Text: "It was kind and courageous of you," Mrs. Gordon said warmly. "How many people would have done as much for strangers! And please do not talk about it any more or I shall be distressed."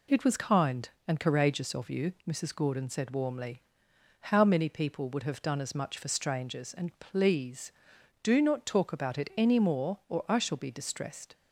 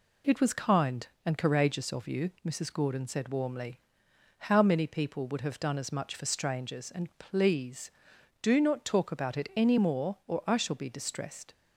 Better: neither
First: none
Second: none

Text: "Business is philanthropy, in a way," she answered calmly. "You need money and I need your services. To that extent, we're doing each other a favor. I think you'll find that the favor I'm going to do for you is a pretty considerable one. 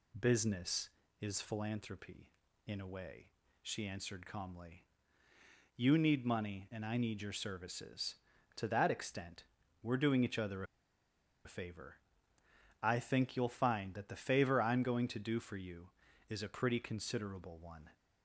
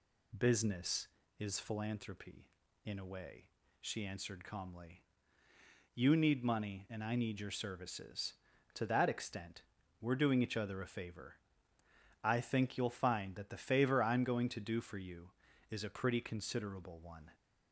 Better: second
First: pauses between "other" and "a"; noticeable; at 10.6 s; 0.81 s long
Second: none

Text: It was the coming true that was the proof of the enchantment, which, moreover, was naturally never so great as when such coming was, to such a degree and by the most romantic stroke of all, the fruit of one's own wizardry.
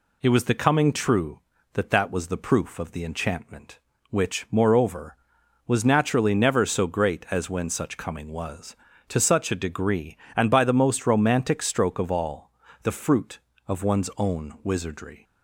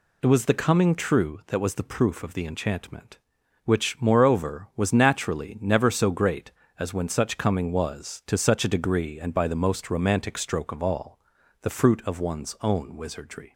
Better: second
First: says "that" twice; at 1.8 s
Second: none

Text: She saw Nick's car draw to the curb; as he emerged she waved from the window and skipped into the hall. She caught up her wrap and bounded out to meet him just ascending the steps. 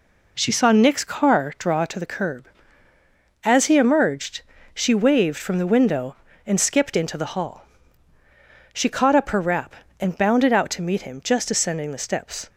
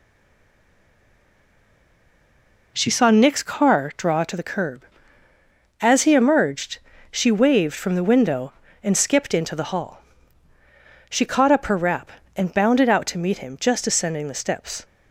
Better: first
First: pauses between "emerged" and "she"; slight; at 4.4 s; 0.32 s long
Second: stays silent before the first word; strong; until 2.7 s; 2.7 s long // pauses between "emerged" and "she"; slight; at 6.7 s; 0.32 s long

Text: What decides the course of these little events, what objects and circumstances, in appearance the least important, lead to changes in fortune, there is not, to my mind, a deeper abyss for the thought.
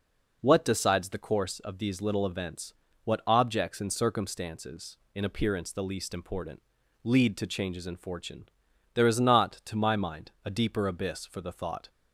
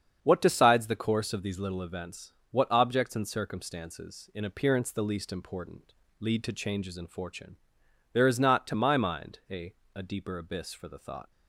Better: first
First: none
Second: starts louder than the rest; strong; until 1.2 s; 7.5 dB // says "a" twice; at 9.9 s

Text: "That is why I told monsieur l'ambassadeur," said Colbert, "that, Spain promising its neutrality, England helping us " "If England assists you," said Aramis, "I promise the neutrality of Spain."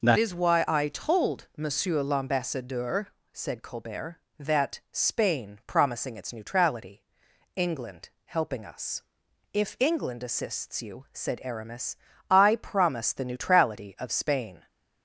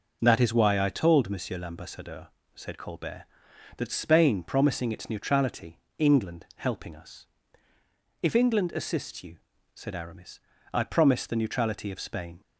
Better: second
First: changes voice at "is"; from 0.1 s on; 14.5 s long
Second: none

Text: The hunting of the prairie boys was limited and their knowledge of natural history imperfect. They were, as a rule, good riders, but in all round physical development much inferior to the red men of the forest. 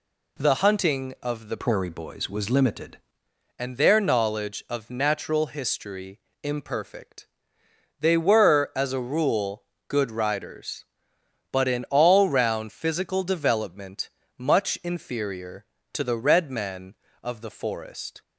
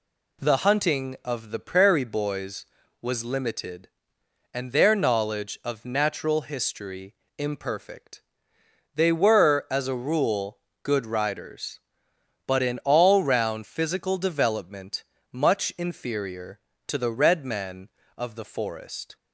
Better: second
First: changes voice from "prairie" to "limited"; from 1.5 to 2.9 s; 1.4 s long // pauses between "history" and "imperfect"; slight; at 6.1 s; 0.24 s long // pauses between "development" and "much"; slight; at 14.0 s; 0.30 s long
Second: pauses between "history" and "imperfect"; slight; at 7.1 s; 0.24 s long // pauses between "development" and "much"; slight; at 15.0 s; 0.30 s long

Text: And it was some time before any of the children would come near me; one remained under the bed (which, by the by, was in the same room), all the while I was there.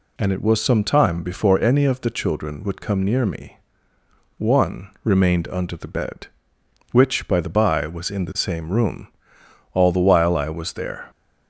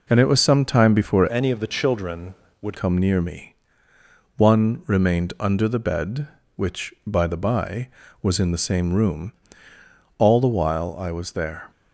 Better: first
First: none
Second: changes voice from "any" to "would"; from 1.3 to 2.7 s; 1.4 s long

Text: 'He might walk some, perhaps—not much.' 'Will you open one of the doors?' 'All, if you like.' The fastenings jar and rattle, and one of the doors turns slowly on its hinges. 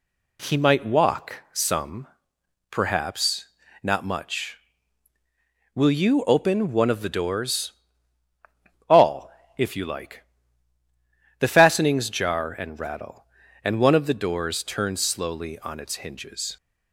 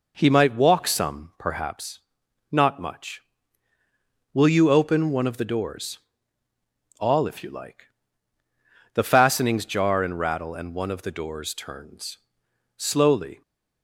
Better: first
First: none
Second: pauses between "turns" and "slowly"; noticeable; at 12.1 s; 0.62 s long // stops before "on its hinges"; at 13.4 s

